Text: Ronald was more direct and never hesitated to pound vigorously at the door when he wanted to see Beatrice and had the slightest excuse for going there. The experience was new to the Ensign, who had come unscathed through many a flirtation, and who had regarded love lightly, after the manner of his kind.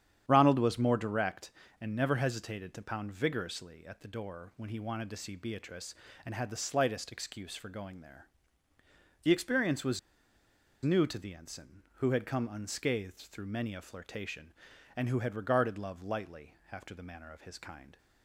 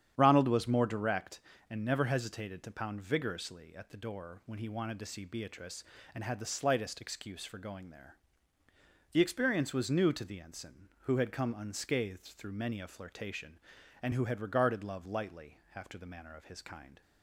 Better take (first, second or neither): second